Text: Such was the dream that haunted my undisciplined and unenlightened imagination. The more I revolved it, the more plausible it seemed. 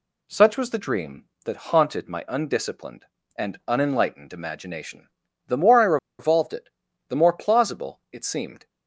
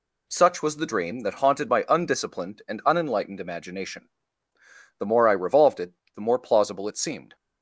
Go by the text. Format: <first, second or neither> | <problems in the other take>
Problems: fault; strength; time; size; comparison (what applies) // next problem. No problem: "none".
second | pauses between "I" and "revolved"; slight; at 5.9 s; 0.22 s long